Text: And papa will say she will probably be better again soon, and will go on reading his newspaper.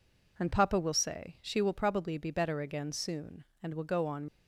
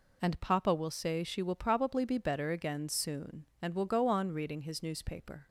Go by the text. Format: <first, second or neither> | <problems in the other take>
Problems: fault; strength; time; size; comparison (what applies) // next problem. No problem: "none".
second | stops before "reading his newspaper"; at 4.2 s